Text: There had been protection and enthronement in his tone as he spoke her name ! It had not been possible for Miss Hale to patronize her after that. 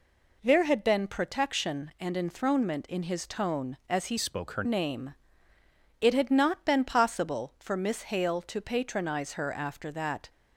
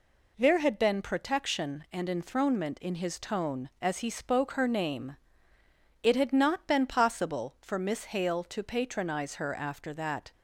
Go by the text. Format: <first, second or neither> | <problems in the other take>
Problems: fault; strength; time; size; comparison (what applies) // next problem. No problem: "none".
second | changes voice from "spoke" to "her"; from 4.1 to 4.6 s; 0.5 s long